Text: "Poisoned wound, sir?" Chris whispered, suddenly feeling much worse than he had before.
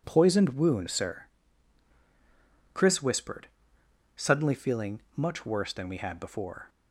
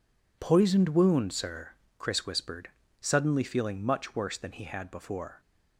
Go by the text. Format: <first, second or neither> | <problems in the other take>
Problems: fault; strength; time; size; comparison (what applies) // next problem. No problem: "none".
second | pauses between "feeling" and "much"; slight; at 5.0 s; 0.16 s long // says "we" for "he"; at 5.8 s